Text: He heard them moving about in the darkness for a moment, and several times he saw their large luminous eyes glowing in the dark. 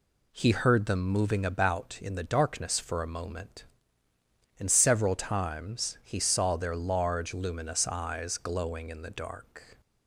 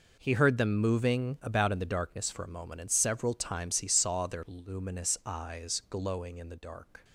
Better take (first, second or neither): first